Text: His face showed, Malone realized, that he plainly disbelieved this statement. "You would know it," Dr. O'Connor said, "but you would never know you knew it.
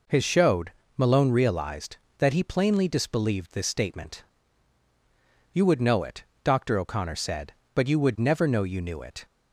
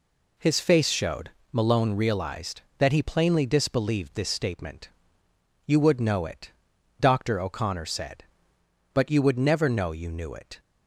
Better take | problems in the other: second | skips "face"; at 0.2 s

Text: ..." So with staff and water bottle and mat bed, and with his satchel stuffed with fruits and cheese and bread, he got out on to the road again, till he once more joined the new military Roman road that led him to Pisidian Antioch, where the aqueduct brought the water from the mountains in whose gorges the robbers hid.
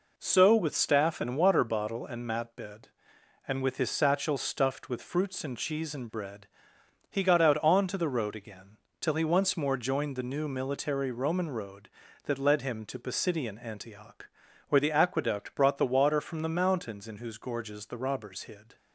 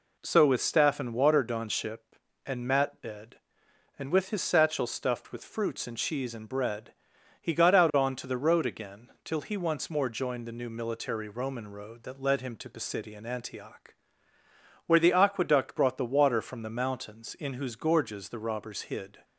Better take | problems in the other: first | says "donship" for "bottle"; at 1.4 s

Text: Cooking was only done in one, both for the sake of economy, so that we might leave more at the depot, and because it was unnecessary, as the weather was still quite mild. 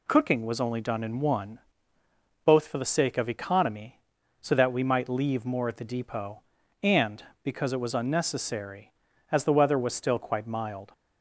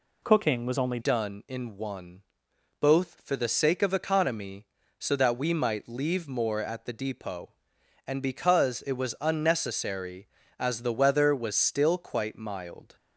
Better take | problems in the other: first | changes voice at "done"; from 1.0 s on; 11.9 s long

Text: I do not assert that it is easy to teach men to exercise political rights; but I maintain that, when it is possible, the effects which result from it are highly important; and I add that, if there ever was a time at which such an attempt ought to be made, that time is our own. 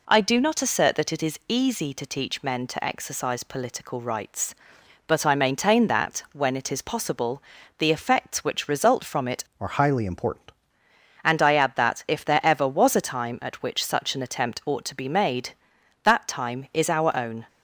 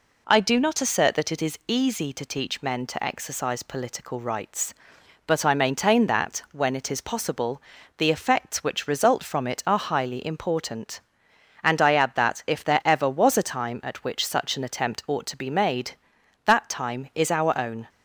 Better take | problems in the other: second | changes voice from "are" to "important"; from 9.5 to 10.5 s; 1.0 s long

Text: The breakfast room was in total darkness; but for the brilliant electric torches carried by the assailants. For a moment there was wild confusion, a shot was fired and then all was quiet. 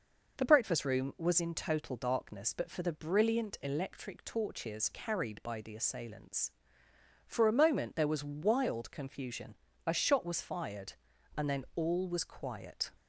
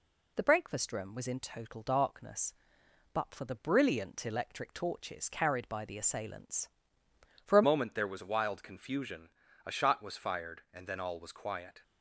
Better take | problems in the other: first | changes voice at "moment"; from 7.6 s on; 4.2 s long

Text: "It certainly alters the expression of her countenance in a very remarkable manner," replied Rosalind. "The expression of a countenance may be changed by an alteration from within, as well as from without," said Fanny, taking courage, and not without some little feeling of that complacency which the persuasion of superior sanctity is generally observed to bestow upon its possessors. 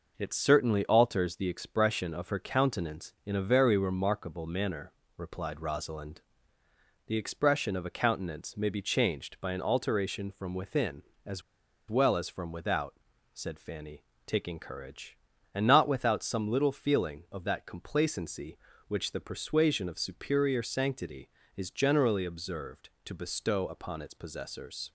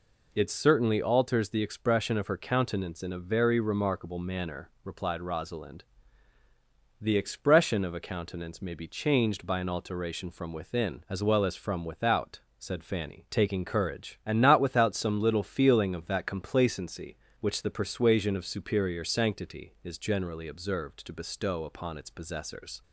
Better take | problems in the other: second | pauses between "as" and "well"; noticeable; at 11.4 s; 0.47 s long

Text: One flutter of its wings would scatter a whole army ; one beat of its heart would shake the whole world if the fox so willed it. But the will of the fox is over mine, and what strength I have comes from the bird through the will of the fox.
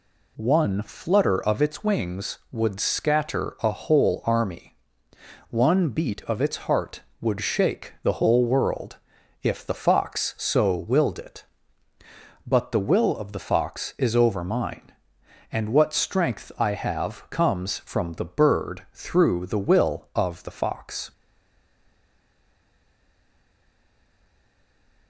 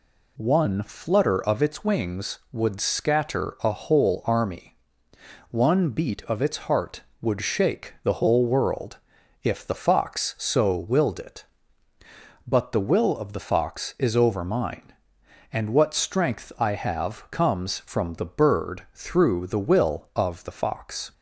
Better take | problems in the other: second | pauses between "world" and "if"; at 8.9 s; 0.44 s long; also in the second // stays silent after the last word; strong; from 21.1 s on; 3.9 s long

